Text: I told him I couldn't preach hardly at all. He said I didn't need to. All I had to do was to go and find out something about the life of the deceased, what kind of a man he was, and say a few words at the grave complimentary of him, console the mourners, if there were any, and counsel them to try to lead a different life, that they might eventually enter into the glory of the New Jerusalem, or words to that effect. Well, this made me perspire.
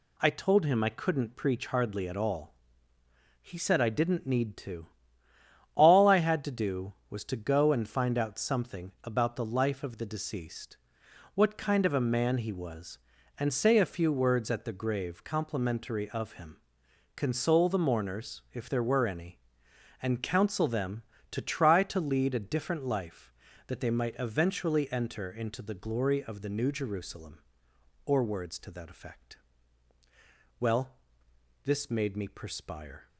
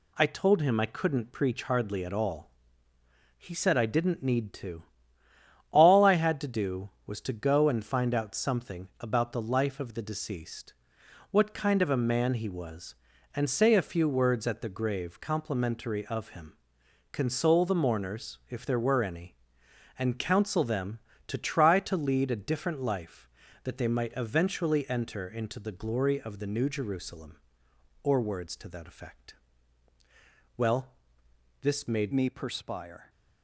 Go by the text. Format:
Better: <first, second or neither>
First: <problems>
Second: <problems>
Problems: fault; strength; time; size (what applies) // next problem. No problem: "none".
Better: first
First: none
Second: changes voice at "me"; from 32.1 s on; 0.9 s long